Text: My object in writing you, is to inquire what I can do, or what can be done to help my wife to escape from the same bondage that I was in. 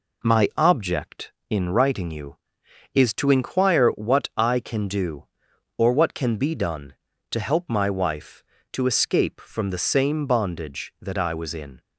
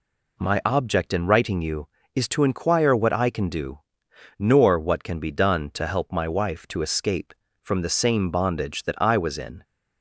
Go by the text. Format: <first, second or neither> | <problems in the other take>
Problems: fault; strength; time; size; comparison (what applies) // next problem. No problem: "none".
first | says "nor" for "or"; at 4.3 s